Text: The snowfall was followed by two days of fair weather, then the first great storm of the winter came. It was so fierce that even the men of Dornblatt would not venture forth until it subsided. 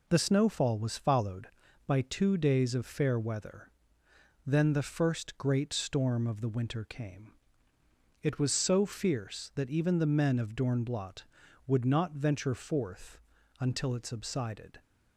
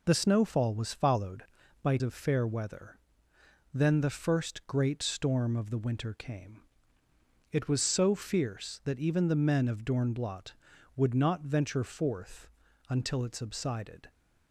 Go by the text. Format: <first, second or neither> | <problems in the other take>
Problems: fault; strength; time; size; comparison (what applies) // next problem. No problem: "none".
first | skips "two days"; at 2.0 s // pauses between "forth" and "until"; at 12.4 s; 0.44 s long; also in the first